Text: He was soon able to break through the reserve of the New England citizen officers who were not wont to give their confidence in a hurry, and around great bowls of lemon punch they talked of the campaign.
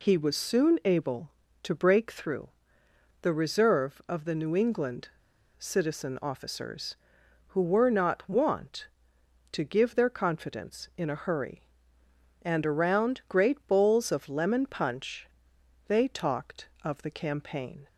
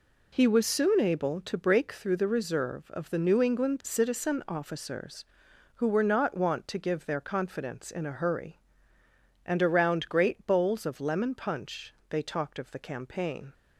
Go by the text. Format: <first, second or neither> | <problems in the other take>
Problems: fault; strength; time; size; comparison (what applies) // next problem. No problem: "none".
second | pauses between "through" and "the"; noticeable; at 2.4 s; 0.72 s long // pauses between "England" and "citizen"; noticeable; at 5.0 s; 0.49 s long // pauses between "punch" and "they"; noticeable; at 15.2 s; 0.58 s long; slight in the second